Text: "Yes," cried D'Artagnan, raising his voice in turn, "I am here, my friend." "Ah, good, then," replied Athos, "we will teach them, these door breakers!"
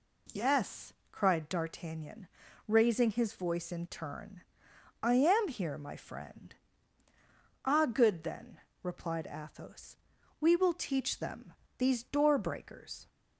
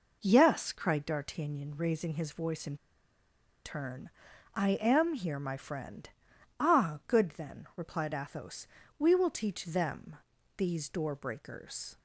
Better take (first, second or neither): first